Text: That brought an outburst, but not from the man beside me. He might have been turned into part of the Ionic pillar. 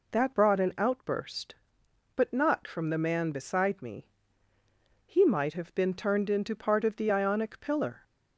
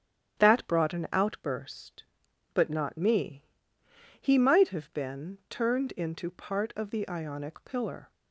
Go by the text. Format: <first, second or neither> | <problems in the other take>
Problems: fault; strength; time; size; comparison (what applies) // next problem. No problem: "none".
first | starts louder than the rest; strong; until 1.4 s; 10 dB // skips "from the man beside"; at 2.9 s